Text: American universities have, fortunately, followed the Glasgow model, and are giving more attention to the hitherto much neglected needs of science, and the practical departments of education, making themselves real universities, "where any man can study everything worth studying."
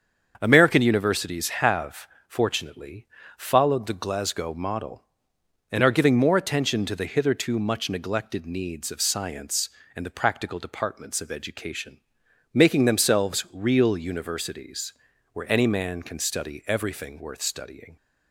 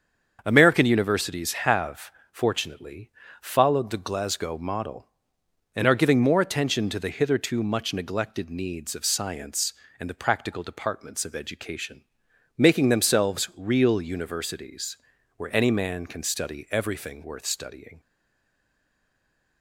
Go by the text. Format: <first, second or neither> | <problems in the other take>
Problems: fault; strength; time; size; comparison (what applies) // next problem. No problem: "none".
first | starts louder than the rest; until 1.4 s; 7 dB; also in the first // stays silent after the last word; noticeable; from 17.9 s on; 1.7 s long